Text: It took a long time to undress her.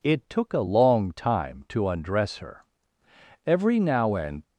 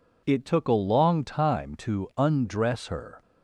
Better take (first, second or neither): second